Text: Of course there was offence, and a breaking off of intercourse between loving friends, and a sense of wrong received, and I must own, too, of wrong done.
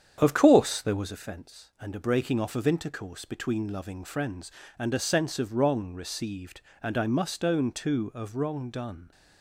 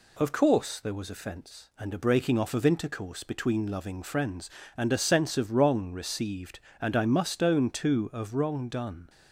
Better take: second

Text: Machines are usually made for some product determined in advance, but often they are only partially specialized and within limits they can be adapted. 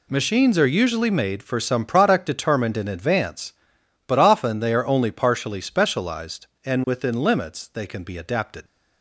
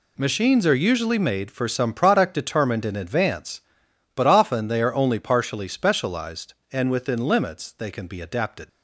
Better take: neither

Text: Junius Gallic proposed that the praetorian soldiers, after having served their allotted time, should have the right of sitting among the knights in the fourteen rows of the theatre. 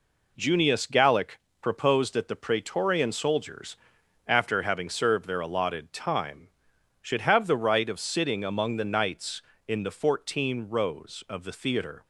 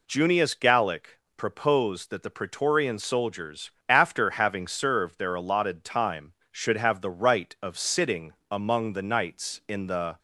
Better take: first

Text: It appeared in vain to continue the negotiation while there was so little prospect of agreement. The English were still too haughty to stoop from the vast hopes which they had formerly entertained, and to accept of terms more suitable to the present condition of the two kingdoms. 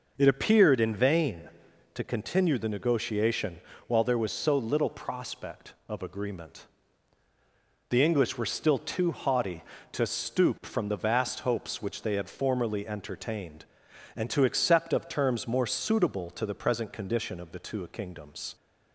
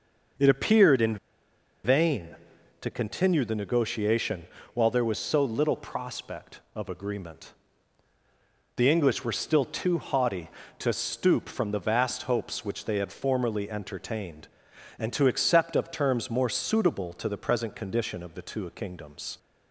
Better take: first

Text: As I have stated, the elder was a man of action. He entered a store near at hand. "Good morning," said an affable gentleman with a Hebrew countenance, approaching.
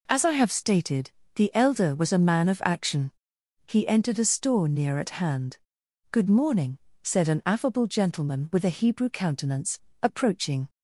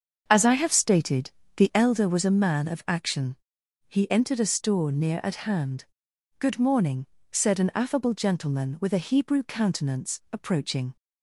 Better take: first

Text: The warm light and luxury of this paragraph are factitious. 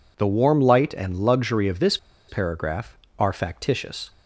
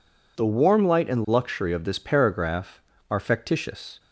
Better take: second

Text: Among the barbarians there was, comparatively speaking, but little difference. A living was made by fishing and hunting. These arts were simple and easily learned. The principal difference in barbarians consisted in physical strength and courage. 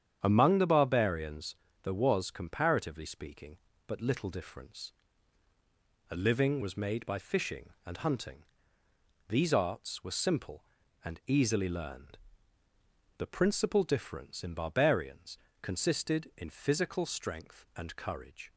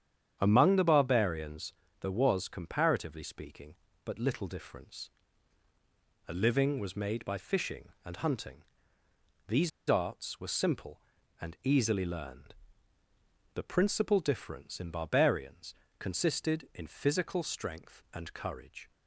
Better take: first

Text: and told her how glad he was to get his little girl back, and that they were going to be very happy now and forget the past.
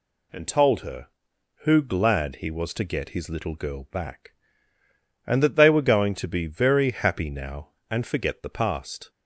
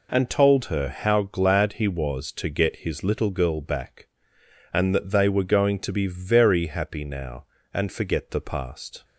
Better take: second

